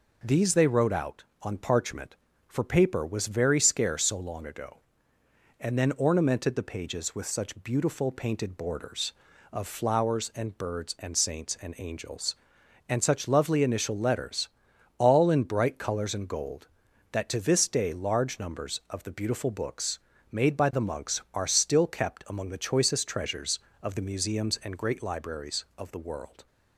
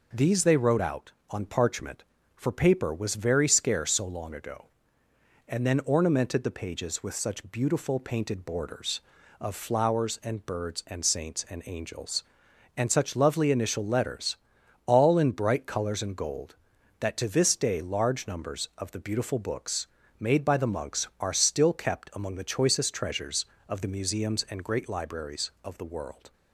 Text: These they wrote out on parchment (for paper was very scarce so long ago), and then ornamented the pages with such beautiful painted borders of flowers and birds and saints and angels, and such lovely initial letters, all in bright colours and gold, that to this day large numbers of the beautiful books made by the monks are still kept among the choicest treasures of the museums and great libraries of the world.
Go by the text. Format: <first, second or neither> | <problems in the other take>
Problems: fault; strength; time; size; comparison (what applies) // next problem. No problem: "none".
neither | pauses between "books" and "made"; slight; the same in both